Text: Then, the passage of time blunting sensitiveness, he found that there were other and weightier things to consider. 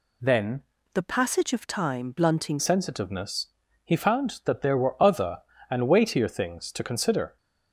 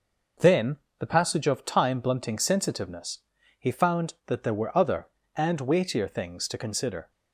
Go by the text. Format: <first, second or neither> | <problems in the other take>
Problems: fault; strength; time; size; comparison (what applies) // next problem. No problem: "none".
second | changes voice from "the" to "blunting"; from 0.9 to 2.5 s; 1.6 s long